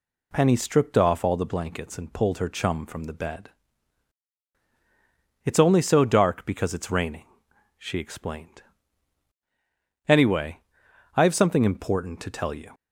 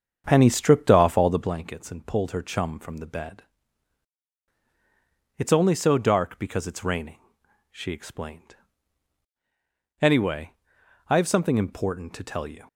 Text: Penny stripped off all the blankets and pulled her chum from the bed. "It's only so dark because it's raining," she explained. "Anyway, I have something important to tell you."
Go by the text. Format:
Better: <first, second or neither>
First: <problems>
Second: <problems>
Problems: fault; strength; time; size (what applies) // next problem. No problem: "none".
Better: first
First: none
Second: starts louder than the rest; strong; until 1.6 s; 7.5 dB